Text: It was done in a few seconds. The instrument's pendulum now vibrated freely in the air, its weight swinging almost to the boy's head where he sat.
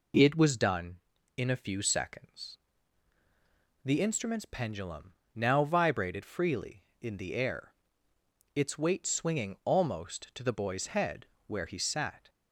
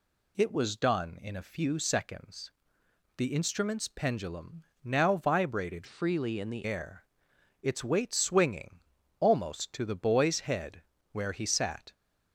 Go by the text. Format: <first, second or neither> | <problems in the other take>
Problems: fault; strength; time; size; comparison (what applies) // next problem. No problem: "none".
first | pauses between "pendulum" and "now"; slight; at 4.6 s; 0.18 s long; slight in the first // changes voice from "freely" to "the"; from 5.8 to 6.6 s; 0.8 s long // pauses between "swinging" and "almost"; at 8.7 s; 0.40 s long // pauses between "head" and "where"; slight; at 10.8 s; 0.30 s long; slight in the first